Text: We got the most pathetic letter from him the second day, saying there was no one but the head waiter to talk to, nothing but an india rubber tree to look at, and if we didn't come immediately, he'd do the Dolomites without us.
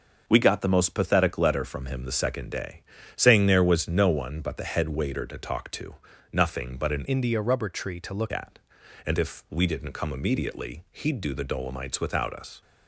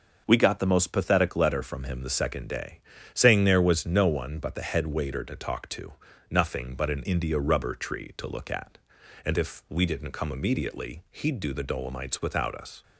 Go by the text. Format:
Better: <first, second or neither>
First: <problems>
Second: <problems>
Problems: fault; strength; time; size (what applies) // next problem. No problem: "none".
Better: second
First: starts louder than the rest; until 1.2 s; 6 dB // changes voice from "india" to "look"; from 7.0 to 8.3 s; 1.3 s long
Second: starts louder than the rest; noticeable; until 1.2 s; 6 dB